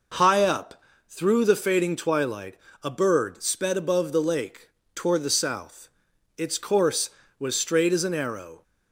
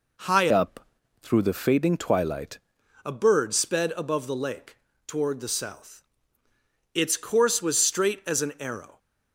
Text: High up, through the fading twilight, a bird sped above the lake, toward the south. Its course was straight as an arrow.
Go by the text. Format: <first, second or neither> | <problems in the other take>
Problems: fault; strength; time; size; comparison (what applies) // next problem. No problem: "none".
first | changes voice from "up" to "twilight"; from 0.5 to 2.5 s; 2.0 s long